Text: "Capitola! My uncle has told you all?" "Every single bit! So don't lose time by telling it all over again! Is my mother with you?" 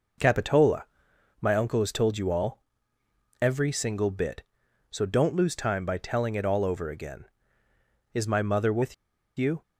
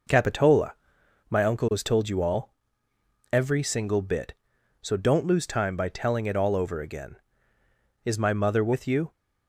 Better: second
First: pauses between "with" and "you"; at 8.9 s; 0.43 s long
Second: none

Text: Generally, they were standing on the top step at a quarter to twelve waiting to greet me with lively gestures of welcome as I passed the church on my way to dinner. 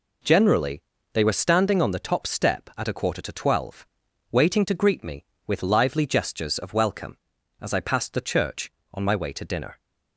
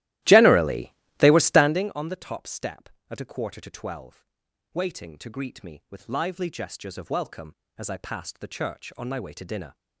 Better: first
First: pauses between "twelve" and "waiting"; at 3.8 s; 0.44 s long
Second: starts louder than the rest; strong; until 1.9 s; 15.5 dB // pauses between "twelve" and "waiting"; noticeable; at 4.2 s; 0.48 s long

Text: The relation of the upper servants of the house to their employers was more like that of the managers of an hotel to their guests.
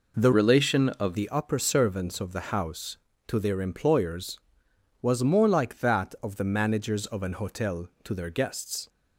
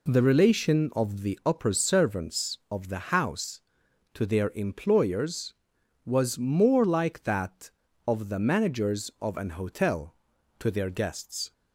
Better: second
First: changes voice from "relation" to "of"; from 0.3 to 1.1 s; 0.8 s long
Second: none

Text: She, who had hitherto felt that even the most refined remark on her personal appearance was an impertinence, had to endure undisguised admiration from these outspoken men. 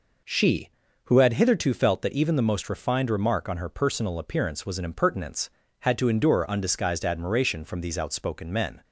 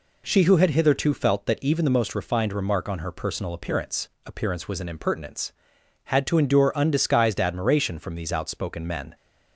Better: first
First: none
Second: says "appearance" twice; at 4.2 s

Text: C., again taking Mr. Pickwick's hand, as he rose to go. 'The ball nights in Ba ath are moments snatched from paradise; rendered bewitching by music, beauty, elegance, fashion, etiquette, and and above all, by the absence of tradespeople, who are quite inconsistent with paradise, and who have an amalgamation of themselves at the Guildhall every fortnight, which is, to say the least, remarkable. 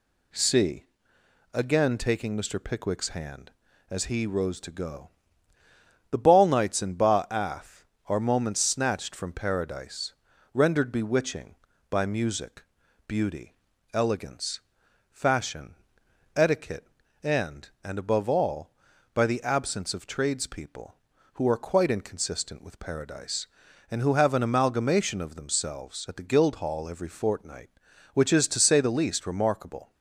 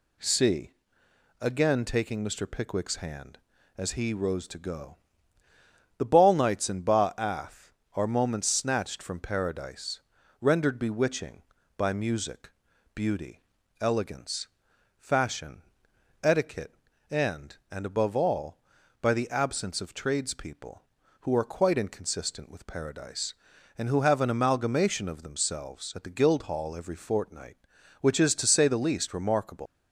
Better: first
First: none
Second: leaves "remarkable" unfinished; at 29.6 s; 135 ms

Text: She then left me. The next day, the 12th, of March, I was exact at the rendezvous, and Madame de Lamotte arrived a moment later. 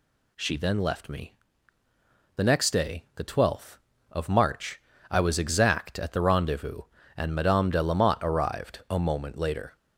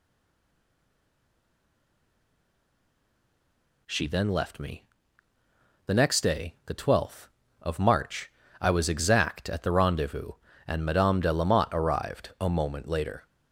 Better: first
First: none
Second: stays silent before the first word; strong; until 3.8 s; 3.8 s long

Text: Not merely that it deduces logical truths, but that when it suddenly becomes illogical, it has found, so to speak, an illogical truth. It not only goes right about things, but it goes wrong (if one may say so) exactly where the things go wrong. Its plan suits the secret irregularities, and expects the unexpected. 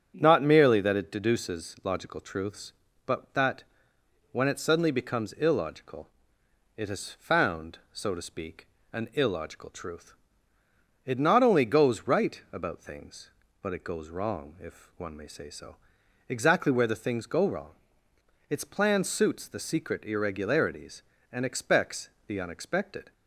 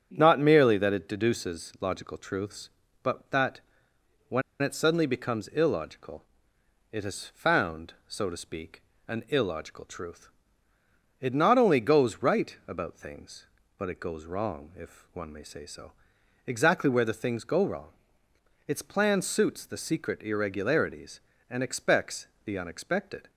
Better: first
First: starts louder than the rest; strong; until 1.1 s; 8.5 dB // pauses between "that" and "when"; noticeable; at 3.6 s; 0.66 s long // pauses between "expects" and "the"; slight; at 22.0 s; 0.16 s long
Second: starts louder than the rest; strong; until 1.1 s; 8.5 dB // pauses between "that" and "when"; noticeable; at 3.6 s; 0.66 s long // pauses between "when" and "it"; slight; at 4.4 s; 0.20 s long // pauses between "expects" and "the"; slight; at 22.2 s; 0.16 s long

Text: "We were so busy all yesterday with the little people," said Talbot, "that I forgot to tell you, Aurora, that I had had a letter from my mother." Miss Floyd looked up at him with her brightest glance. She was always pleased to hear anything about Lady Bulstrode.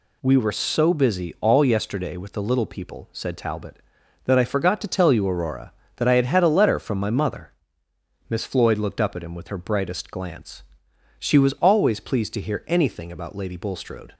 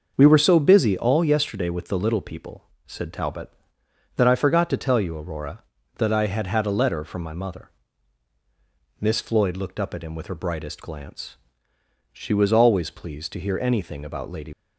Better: first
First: none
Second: starts louder than the rest; noticeable; until 1.1 s; 6 dB // stops before "Bulstrode"; at 14.5 s

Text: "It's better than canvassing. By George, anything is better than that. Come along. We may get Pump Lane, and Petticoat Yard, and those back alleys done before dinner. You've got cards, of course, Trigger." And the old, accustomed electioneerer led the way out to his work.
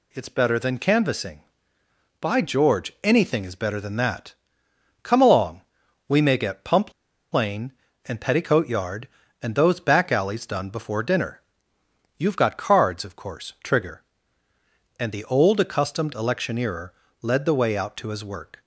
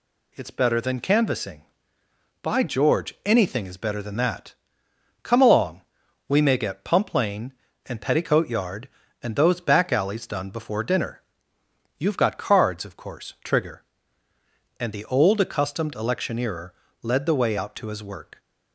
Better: second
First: pauses between "Pump" and "Lane"; at 6.9 s; 0.39 s long // pauses between "electioneerer" and "led"; slight; at 16.9 s; 0.32 s long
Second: pauses between "electioneerer" and "led"; slight; at 16.7 s; 0.32 s long

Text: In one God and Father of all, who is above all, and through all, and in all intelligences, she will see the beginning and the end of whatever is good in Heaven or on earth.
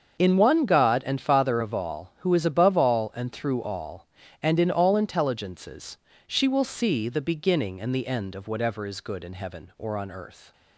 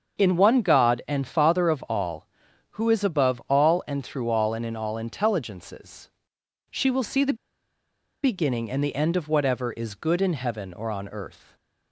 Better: first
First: starts louder than the rest; until 1.2 s; 7 dB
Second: starts louder than the rest; until 1.2 s; 7 dB // pauses between "the" and "beginning"; noticeable; at 7.3 s; 0.88 s long

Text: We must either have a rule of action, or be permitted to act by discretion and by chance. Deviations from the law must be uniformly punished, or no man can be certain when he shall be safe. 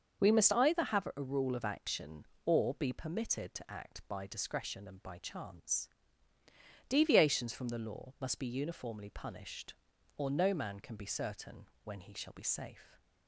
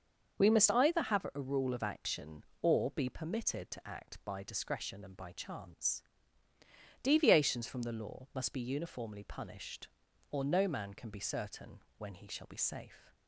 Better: neither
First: starts louder than the rest; until 1.2 s; 6.5 dB // pauses between "certain" and "when"; slight; at 11.6 s; 0.18 s long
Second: starts louder than the rest; until 1.3 s; 6.5 dB // pauses between "certain" and "when"; slight; at 11.8 s; 0.18 s long

